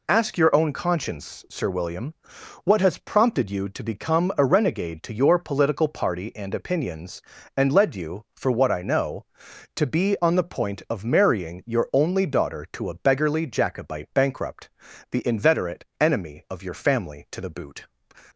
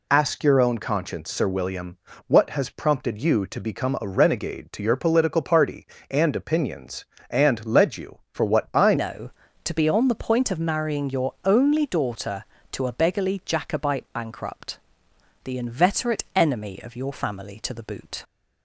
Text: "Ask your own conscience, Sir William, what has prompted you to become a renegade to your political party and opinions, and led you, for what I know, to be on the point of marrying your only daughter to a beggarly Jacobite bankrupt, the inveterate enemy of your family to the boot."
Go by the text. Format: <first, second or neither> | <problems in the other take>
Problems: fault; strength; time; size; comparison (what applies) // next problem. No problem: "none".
first | changes voice at "know"; from 8.9 s on; 9.3 s long